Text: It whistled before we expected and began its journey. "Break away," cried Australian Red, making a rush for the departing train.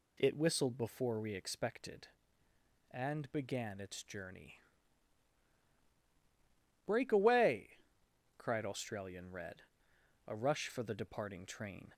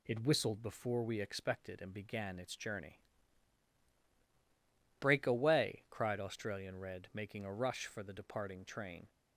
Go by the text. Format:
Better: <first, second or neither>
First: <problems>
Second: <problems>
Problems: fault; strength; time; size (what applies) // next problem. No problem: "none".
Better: second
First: skips "making"; at 9.9 s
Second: none